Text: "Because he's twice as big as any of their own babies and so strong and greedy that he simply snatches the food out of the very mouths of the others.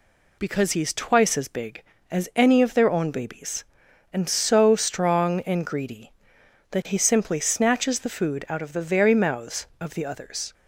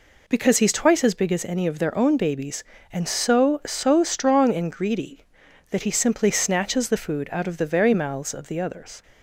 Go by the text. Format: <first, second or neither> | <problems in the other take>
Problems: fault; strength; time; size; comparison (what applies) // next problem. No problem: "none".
first | says "so" twice; at 3.6 s